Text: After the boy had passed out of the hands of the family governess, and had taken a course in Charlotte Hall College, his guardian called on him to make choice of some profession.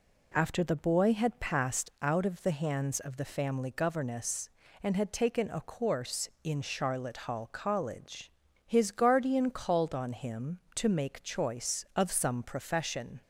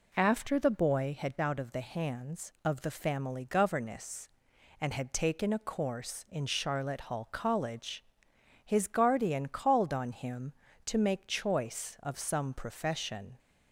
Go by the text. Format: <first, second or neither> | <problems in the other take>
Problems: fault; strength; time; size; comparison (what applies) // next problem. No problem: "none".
first | skips "passed"; at 1.3 s